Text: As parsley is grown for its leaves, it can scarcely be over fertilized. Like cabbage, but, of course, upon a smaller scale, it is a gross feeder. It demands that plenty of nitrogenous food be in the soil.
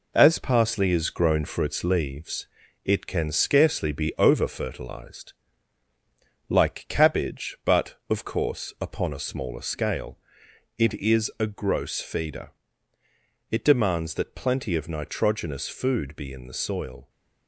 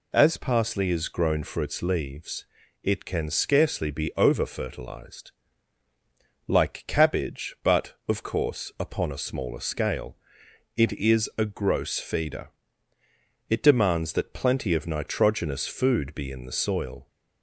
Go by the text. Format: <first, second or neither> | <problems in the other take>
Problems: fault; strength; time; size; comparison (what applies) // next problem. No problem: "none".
second | gets quieter; noticeable; throughout; 5.5 dB